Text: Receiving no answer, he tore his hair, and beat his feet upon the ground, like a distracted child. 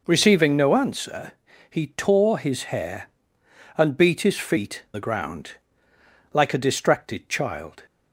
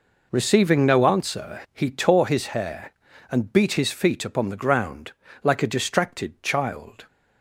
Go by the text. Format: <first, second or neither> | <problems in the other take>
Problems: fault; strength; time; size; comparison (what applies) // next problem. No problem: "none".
second | skips "upon"; at 4.8 s